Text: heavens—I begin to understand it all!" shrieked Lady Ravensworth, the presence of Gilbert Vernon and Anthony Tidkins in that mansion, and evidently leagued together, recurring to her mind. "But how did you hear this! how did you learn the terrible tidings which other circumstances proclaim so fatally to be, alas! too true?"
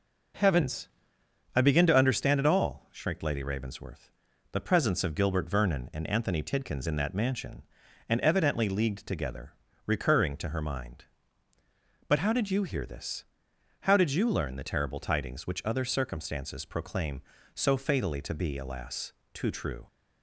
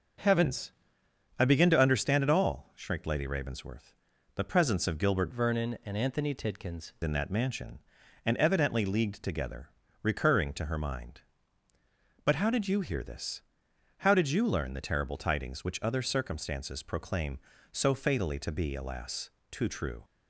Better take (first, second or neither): first